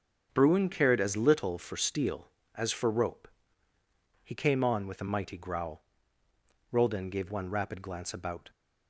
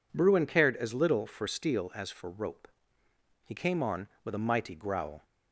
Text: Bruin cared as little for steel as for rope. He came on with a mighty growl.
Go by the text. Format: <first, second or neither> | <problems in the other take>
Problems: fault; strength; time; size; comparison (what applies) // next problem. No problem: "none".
second | starts louder than the rest; strong; until 1.3 s; 7 dB // goes on to say "Roldan gave one rapid glance about"; strong; from 6.7 s on; 1.8 s long